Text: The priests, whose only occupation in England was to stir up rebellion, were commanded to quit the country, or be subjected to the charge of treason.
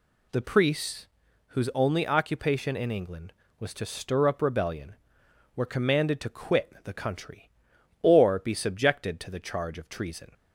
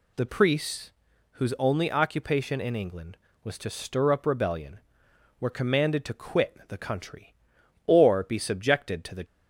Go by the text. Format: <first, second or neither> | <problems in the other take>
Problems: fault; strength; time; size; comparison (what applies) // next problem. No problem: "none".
first | stops before "charge of treason"; at 9.2 s